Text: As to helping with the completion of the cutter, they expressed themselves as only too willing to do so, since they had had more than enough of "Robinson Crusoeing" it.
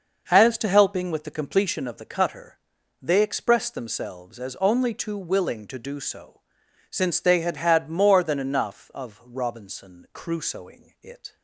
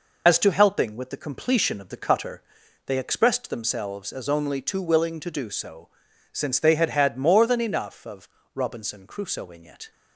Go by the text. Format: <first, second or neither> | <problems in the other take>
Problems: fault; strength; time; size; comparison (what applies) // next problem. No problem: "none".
first | loses the start of "As"; at 0.2 s; 50 ms // pauses between "of" and "Robinson"; slight; at 8.2 s; 0.26 s long